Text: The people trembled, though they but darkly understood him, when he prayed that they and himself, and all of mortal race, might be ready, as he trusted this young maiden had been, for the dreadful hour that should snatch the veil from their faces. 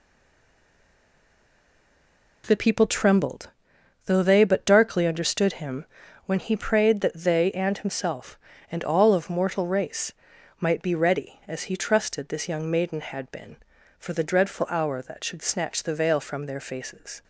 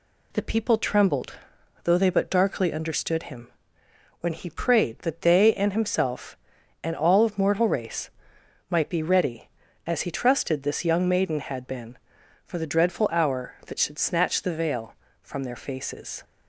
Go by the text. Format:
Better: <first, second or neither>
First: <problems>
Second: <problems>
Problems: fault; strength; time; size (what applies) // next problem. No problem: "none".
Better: second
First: stays silent before the first word; until 2.4 s; 2.4 s long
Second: none